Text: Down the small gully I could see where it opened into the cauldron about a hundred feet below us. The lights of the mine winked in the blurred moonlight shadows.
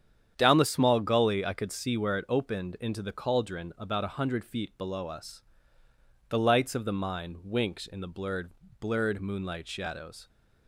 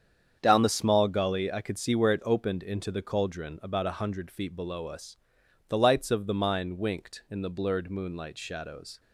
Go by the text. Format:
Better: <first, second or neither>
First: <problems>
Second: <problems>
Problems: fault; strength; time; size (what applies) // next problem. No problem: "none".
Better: second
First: starts louder than the rest; strong; until 1.3 s; 9 dB // says "blurred" twice; at 8.7 s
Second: starts louder than the rest; strong; until 1.4 s; 8 dB